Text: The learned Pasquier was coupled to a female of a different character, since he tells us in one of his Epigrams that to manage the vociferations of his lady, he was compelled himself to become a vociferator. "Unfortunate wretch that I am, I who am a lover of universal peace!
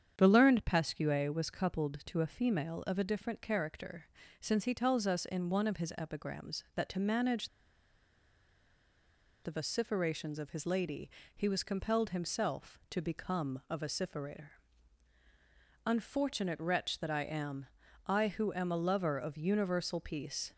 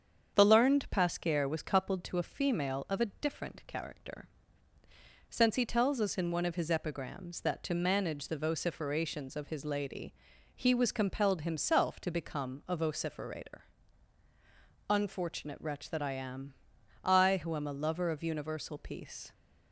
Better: second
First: starts louder than the rest; strong; until 1.1 s; 8 dB // pauses between "manage" and "the"; strong; at 7.4 s; 1.9 s long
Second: starts louder than the rest; strong; until 1.3 s; 7.5 dB

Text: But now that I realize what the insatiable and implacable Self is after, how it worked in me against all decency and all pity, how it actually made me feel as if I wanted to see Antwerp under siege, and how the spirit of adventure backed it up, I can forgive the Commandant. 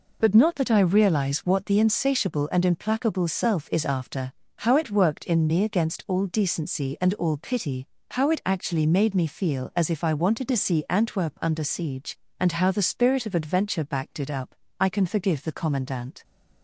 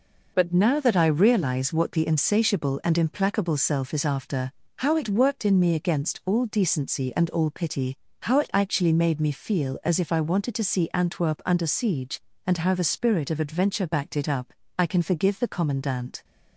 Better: second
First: says "not" for "now"; at 0.3 s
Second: none

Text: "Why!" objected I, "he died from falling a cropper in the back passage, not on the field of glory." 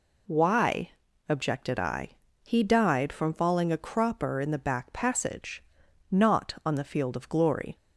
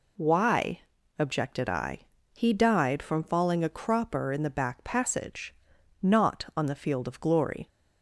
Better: neither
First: none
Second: none

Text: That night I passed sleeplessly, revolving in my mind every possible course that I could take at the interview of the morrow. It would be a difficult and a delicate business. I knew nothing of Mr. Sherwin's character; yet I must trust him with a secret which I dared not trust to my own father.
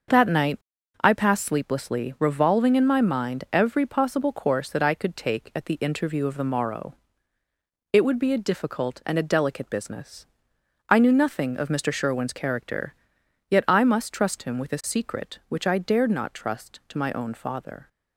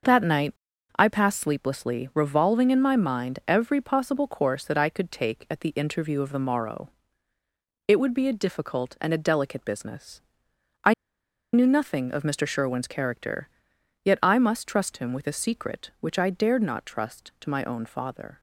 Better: first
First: starts louder than the rest; until 1.5 s; 6.5 dB // pauses between "night" and "I"; noticeable; at 0.5 s; 0.46 s long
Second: starts louder than the rest; until 1.5 s; 6.5 dB // pauses between "night" and "I"; noticeable; at 0.5 s; 0.46 s long // pauses between "I" and "knew"; noticeable; at 10.9 s; 0.61 s long

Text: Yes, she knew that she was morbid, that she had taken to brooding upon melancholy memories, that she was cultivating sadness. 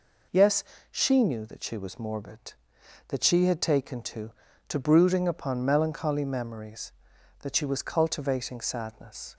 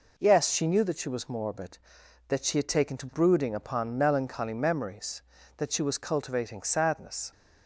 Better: second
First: says "to" twice; at 4.6 s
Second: none

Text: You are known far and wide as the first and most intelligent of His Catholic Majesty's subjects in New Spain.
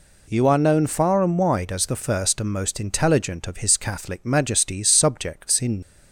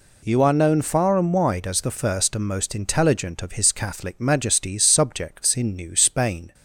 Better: second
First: stops before "New Spain"; at 5.8 s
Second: none

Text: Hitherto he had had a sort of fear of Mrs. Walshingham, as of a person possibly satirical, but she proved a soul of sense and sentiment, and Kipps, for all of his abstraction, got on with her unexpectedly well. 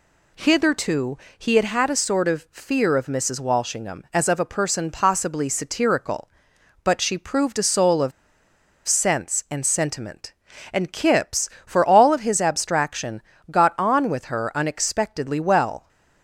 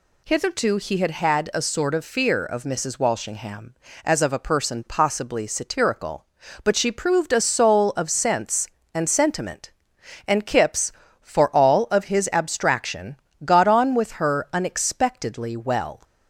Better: second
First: pauses between "Hitherto" and "he"; slight; at 1.1 s; 0.22 s long // pauses between "of" and "sense"; noticeable; at 8.1 s; 0.76 s long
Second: none

